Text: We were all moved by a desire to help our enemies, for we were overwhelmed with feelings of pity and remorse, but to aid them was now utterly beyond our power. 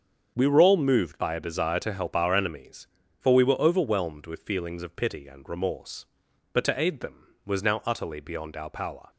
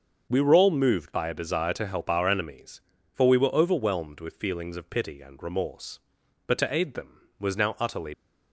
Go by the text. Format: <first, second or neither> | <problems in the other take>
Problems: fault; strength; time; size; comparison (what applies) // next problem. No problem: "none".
first | starts louder than the rest; until 1.3 s; 6.5 dB; strong in the first // stops before "beyond our power"; at 8.1 s